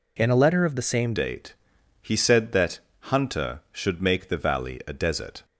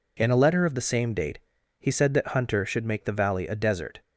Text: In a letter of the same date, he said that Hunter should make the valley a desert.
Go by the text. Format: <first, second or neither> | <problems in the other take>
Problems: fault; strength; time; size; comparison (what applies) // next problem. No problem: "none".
second | changes voice at "date"; from 1.1 s on; 4.3 s long // pauses between "that" and "Hunter"; slight; at 2.7 s; 0.32 s long